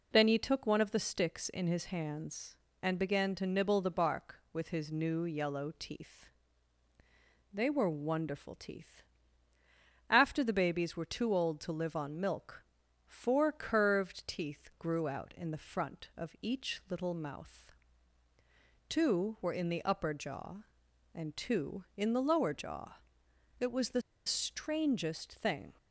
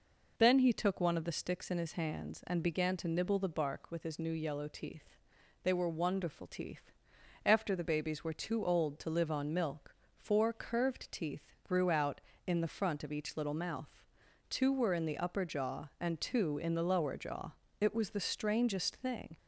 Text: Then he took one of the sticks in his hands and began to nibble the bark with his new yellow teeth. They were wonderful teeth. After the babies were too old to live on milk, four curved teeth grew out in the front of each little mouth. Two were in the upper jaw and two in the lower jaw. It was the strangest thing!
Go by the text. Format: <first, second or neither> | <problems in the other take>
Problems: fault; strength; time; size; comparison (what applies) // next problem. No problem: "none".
second | pauses between "the" and "strangest"; slight; at 24.0 s; 0.25 s long